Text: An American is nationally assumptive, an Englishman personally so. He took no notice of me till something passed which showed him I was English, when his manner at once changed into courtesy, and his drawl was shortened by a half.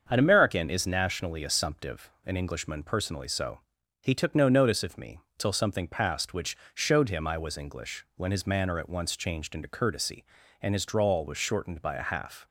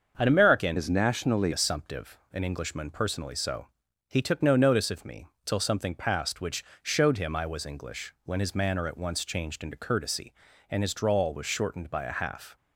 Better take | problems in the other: first | starts louder than the rest; until 1.1 s; 6.5 dB; also in the first // changes voice from "is" to "nationally"; from 0.7 to 1.5 s; 0.8 s long // pauses between "me" and "till"; slight; at 5.2 s; 0.18 s long; slight in the first // pauses between "which" and "showed"; slight; at 6.6 s; 0.20 s long; slight in the first

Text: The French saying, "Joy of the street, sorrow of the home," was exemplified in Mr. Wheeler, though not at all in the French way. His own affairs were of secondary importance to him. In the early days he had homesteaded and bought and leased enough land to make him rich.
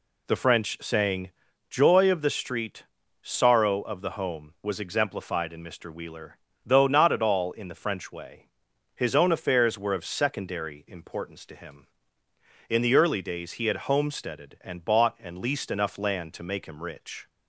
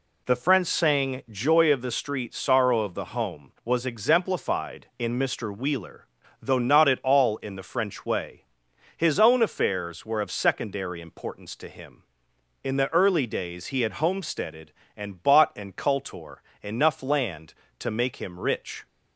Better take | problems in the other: first | says "cultor" for "leased"; at 15.7 s

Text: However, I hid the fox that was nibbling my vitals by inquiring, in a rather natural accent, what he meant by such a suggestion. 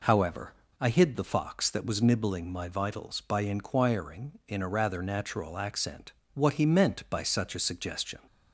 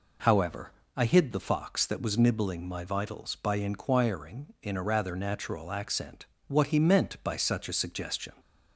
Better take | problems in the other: neither | none

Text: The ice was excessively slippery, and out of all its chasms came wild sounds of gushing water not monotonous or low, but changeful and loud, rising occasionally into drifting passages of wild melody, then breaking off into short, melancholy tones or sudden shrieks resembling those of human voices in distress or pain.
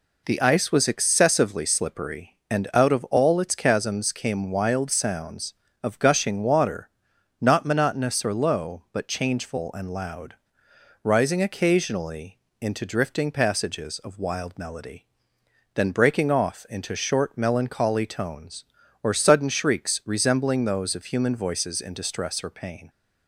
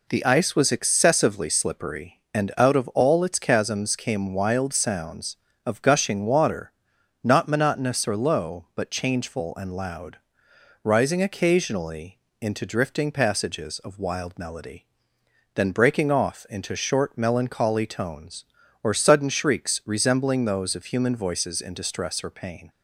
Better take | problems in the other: neither | pauses between "water" and "not"; noticeable; the same in both // pauses between "occasionally" and "into"; slight; the same in both

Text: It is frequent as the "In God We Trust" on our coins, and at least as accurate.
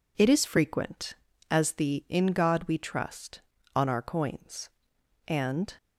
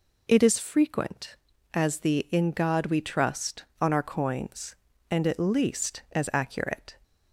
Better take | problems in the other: second | stops before "at least as accurate"; at 5.7 s

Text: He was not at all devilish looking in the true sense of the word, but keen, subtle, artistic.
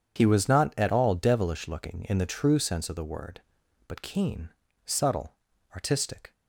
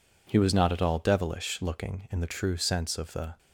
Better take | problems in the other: first | stops before "word but keen subtle artistic"; at 3.3 s

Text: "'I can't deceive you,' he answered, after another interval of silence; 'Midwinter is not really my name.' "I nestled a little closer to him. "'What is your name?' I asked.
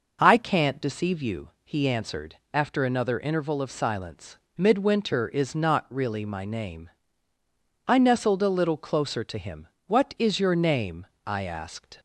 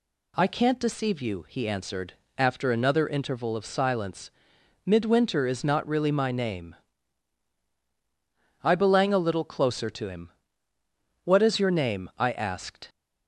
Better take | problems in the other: first | says "belang" for "nestled"; at 8.7 s

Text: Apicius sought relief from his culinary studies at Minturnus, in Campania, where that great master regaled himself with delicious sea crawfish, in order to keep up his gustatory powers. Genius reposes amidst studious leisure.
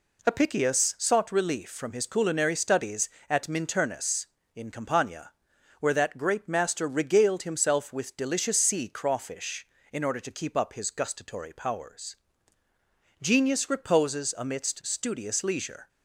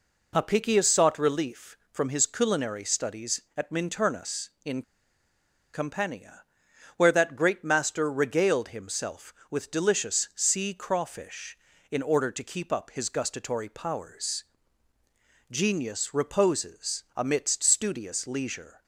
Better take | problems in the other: first | pauses between "in" and "Campania"; noticeable; at 4.8 s; 0.91 s long

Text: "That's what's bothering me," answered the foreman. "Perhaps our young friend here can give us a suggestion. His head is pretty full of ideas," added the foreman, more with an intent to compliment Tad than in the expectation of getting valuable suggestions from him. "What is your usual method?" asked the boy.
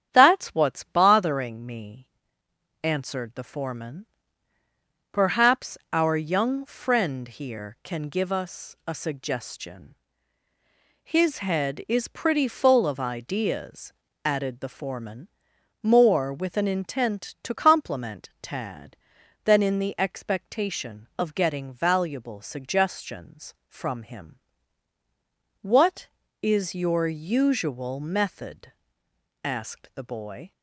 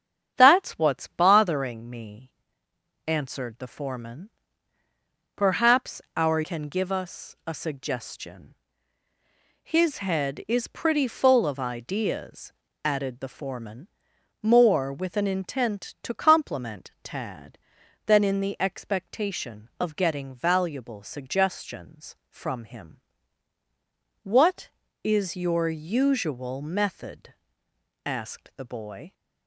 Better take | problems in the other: first | starts louder than the rest; strong; until 1.3 s; 8 dB; strong in the first // skips "young friend here"; at 6.4 s

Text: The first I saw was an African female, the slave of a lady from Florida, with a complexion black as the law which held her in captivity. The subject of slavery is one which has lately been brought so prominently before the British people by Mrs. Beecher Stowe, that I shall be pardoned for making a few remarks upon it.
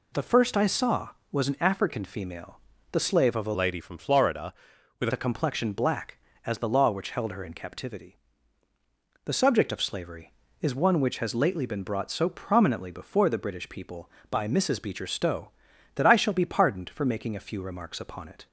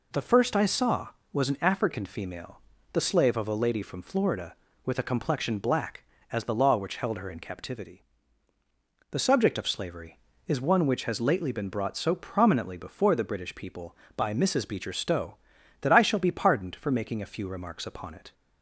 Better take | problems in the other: second | changes voice from "lady" to "with"; from 3.5 to 5.0 s; 1.5 s long

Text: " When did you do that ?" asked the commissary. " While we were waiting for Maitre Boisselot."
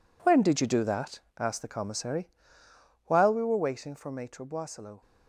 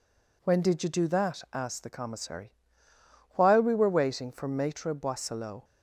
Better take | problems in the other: second | gets quieter; strong; throughout; 10.5 dB

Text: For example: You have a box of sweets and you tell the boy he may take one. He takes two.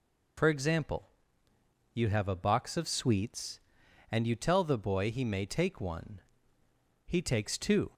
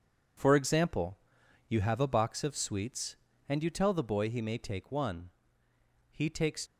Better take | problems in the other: first | stops before "two"; at 6.6 s

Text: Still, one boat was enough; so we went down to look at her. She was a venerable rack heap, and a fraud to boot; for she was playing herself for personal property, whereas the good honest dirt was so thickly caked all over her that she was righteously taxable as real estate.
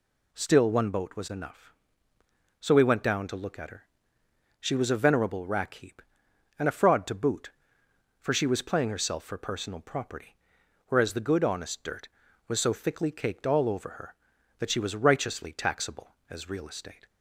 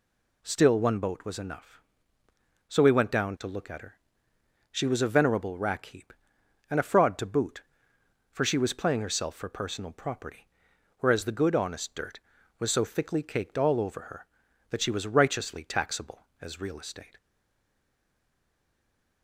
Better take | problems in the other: first | stays silent after the last word; noticeable; from 17.1 s on; 2.1 s long

